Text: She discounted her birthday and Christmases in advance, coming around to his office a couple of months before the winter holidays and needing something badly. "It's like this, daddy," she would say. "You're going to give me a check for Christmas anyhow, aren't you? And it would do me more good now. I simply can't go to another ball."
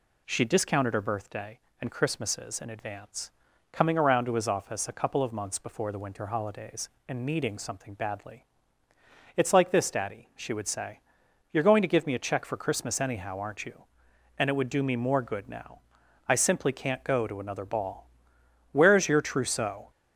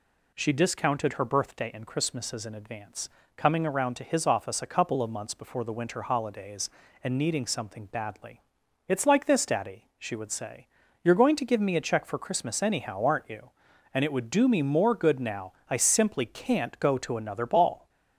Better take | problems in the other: second | goes on to say "Where's your trousseau"; noticeable; from 18.7 s on; 1.1 s long

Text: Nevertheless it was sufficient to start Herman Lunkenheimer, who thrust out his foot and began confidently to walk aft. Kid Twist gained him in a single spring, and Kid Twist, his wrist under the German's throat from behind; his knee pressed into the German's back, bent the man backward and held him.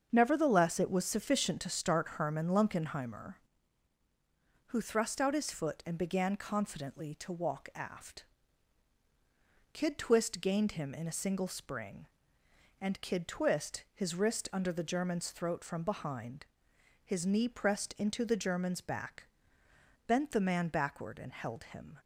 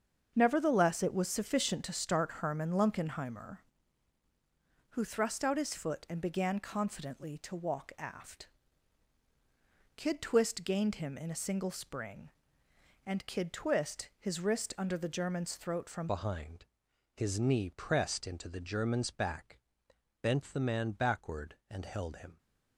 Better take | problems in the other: first | starts louder than the rest; strong; until 1.3 s; 7 dB; strong in the first // changes voice at "behind"; from 16.0 s on; 6.3 s long

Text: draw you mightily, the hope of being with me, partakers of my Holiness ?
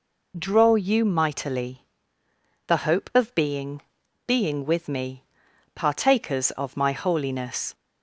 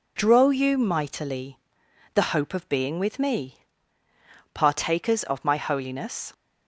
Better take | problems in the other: second | says "being" twice; at 4.2 s

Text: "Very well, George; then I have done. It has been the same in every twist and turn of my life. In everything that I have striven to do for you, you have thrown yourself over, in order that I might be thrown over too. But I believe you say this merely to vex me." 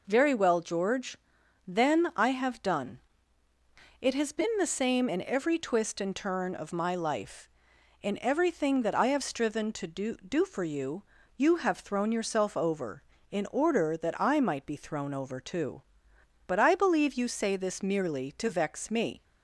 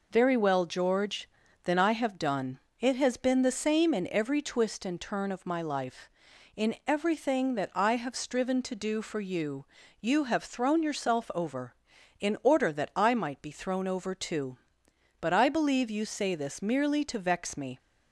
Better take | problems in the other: second | says "do" twice; at 10.1 s

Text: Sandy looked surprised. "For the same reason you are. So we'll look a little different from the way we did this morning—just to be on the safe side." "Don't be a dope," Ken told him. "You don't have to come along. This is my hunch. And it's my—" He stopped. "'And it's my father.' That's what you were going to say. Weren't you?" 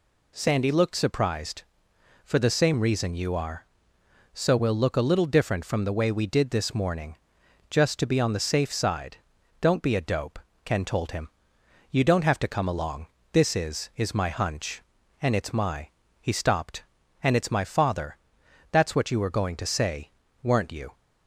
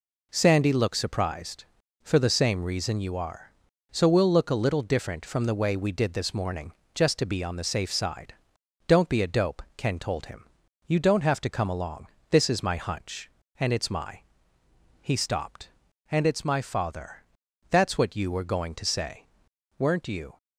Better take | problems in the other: second | says "is" twice; at 13.9 s

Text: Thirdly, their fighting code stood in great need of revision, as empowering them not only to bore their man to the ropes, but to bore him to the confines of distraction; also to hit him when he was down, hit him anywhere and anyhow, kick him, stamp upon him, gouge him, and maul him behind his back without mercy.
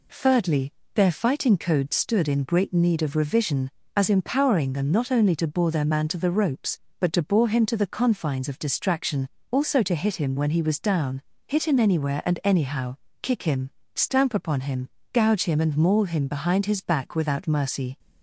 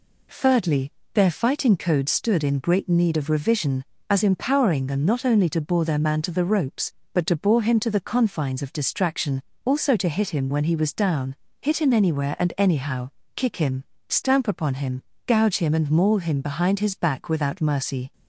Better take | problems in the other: neither | none

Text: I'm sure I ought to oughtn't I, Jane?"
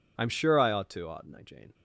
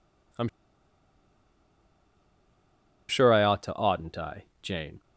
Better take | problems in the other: first | pauses between "I'm" and "sure"; strong; at 0.4 s; 2.6 s long

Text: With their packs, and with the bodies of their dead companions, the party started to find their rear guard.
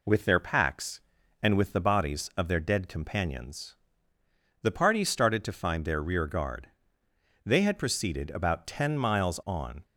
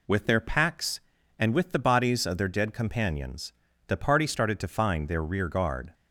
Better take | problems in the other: second | goes on to say "They had proceeded about ten miles on"; strong; from 7.4 s on; 2.3 s long

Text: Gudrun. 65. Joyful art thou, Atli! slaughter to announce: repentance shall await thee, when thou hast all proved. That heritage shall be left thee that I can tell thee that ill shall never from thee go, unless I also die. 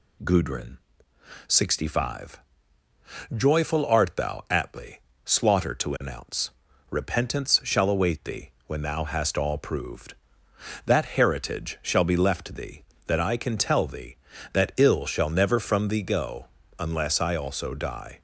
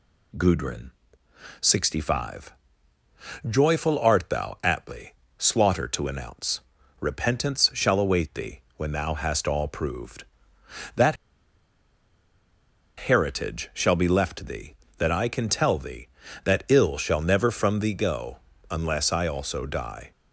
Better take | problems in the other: first | pauses between "That" and "heritage"; strong; at 11.1 s; 1.8 s long

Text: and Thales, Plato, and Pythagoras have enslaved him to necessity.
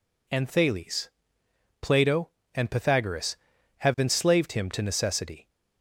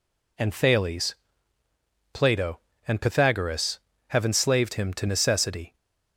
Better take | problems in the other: neither | none

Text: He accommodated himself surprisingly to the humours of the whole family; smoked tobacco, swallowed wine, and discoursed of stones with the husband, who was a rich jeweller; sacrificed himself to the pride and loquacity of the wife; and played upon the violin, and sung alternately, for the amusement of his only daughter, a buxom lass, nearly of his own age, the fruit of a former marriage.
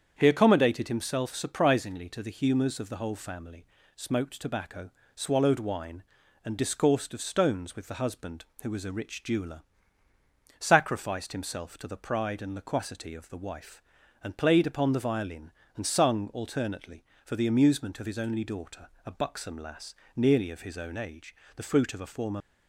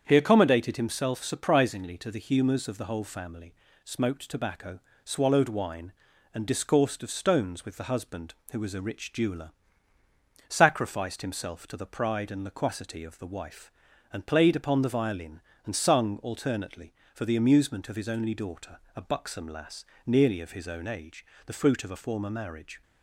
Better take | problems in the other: second | starts louder than the rest; strong; until 1.1 s; 8 dB; strong in the second // stops before "marriage"; at 22.4 s

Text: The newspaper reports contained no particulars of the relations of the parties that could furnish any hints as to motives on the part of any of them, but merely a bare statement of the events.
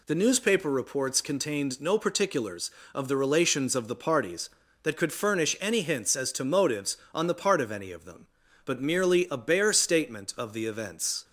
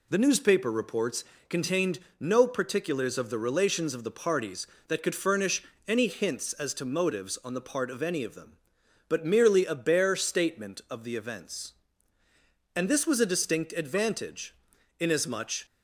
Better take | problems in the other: first | pauses between "reports" and "contained"; slight; at 1.2 s; 0.26 s long // pauses between "contained" and "no"; slight; at 1.9 s; 0.20 s long // pauses between "furnish" and "any"; slight; at 5.6 s; 0.24 s long // goes on to say "And this was a distinct advantage inasmuch"; strong; from 12.7 s on; 2.9 s long

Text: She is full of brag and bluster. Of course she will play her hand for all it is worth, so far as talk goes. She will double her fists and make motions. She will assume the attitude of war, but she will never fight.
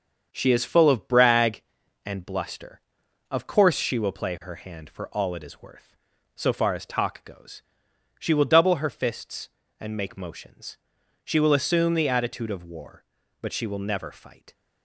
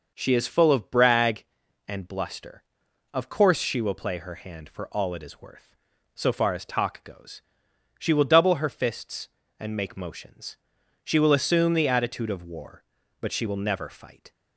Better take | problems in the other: second | gets quieter; noticeable; throughout; 5.5 dB

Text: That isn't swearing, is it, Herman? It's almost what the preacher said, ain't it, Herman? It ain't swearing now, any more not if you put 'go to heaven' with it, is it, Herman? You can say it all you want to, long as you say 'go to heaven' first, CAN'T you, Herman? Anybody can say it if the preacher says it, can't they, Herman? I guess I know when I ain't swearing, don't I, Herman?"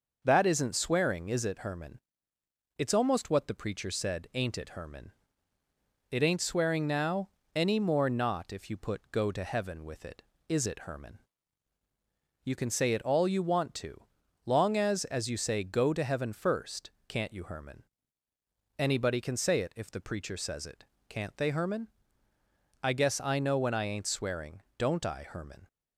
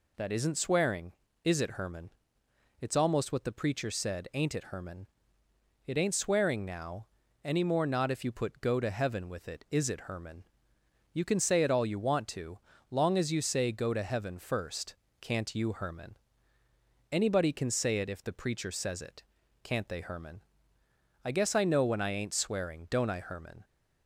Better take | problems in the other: second | says "as" twice; at 15.0 s

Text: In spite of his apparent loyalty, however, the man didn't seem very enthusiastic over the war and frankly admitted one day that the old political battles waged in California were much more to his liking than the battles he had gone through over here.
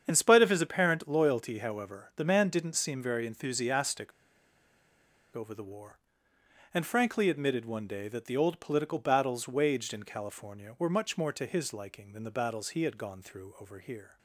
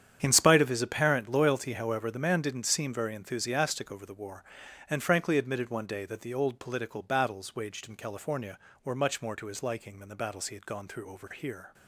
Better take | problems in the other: second | starts louder than the rest; strong; until 1.0 s; 8 dB; strong in the second // pauses between "enthusiastic" and "over"; strong; at 4.1 s; 1.2 s long

